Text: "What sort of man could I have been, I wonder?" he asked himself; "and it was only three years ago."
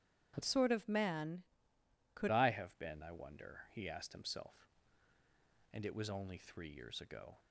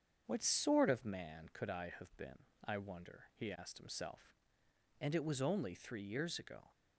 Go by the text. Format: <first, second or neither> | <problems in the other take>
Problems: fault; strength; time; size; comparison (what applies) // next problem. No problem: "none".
second | starts louder than the rest; strong; until 1.3 s; 10.5 dB; strong in the second // changes voice from "sort" to "could"; from 0.4 to 2.2 s; 1.8 s long